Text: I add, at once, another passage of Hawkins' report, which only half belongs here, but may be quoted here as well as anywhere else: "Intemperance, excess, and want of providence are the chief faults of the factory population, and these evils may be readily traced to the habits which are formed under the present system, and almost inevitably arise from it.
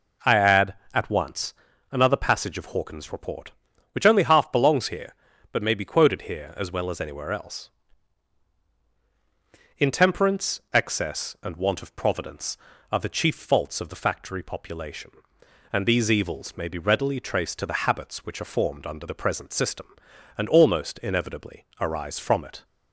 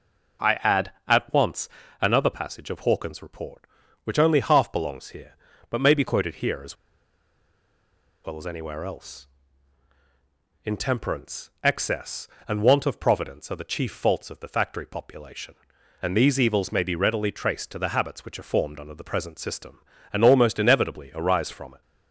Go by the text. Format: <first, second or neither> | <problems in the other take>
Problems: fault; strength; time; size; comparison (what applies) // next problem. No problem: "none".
first | pauses between "as" and "well"; strong; at 6.7 s; 1.5 s long